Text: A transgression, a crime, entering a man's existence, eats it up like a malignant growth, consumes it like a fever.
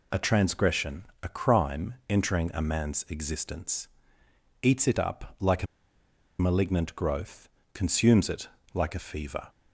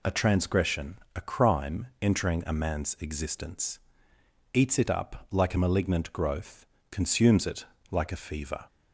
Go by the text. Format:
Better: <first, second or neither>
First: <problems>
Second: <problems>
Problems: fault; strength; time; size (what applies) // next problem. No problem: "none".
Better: second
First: pauses between "a" and "malignant"; noticeable; at 5.6 s; 0.75 s long // pauses between "it" and "like"; slight; at 8.4 s; 0.24 s long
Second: pauses between "it" and "like"; slight; at 7.6 s; 0.24 s long